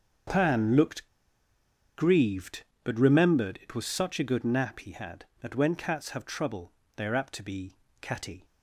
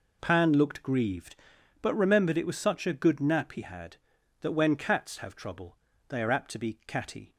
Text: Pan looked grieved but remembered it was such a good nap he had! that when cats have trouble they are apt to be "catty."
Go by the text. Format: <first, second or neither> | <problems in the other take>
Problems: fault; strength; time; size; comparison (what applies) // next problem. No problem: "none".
second | starts louder than the rest; until 2.1 s; 6.5 dB // pauses between "looked" and "grieved"; noticeable; at 1.0 s; 0.88 s long // pauses between "trouble" and "they"; slight; at 6.7 s; 0.26 s long; slight in the second // pauses between "be" and "catty"; slight; at 7.7 s; 0.30 s long